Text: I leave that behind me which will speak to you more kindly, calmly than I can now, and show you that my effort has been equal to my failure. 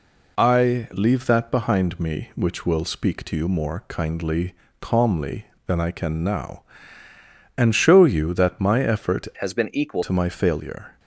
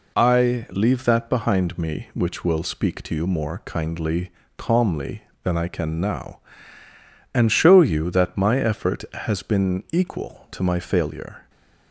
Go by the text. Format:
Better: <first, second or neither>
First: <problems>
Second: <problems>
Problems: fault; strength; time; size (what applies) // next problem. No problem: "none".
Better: second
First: changes voice from "has" to "equal"; from 9.4 to 10.0 s; 0.6 s long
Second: none